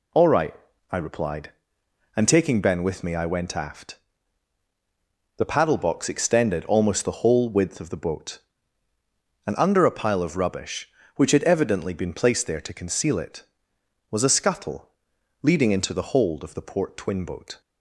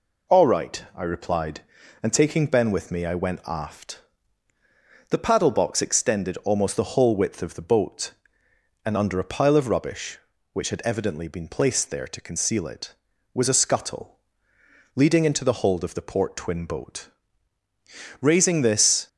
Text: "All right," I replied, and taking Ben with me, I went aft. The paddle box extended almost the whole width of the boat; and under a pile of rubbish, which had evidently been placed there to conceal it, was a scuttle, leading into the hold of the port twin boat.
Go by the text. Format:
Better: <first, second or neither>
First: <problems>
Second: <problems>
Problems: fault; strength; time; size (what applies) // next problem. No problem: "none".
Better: first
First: none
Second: goes on to say "Raising this"; noticeable; from 18.1 s on; 0.88 s long